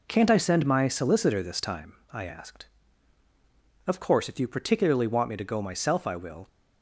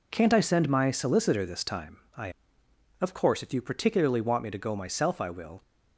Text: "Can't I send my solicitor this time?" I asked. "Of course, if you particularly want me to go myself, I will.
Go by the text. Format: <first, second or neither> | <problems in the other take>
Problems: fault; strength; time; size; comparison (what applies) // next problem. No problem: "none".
first | skips "asked"; at 2.6 s